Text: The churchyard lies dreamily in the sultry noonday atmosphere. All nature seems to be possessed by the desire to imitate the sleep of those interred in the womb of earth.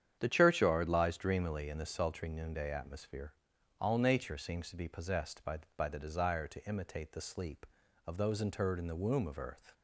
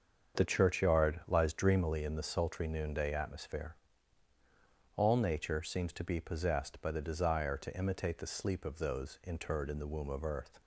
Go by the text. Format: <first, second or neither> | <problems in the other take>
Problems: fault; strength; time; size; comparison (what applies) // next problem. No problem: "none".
second | starts louder than the rest; strong; until 1.2 s; 9 dB; also in the second // says "by" twice; at 5.7 s